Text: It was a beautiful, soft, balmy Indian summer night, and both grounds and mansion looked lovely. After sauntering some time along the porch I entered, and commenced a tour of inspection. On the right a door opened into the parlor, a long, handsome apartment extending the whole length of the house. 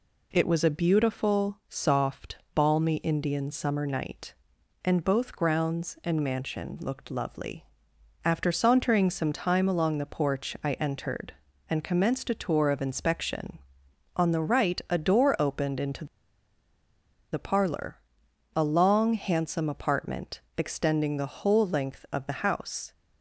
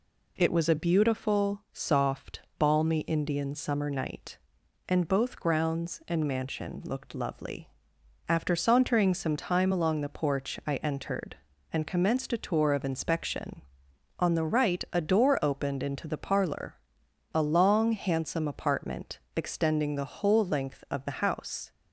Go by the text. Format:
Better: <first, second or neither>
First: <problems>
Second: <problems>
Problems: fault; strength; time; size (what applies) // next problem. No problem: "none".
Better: second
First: pauses between "into" and "the"; strong; at 16.0 s; 1.2 s long // pauses between "apartment" and "extending"; slight; at 20.4 s; 0.18 s long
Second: pauses between "apartment" and "extending"; slight; at 19.1 s; 0.18 s long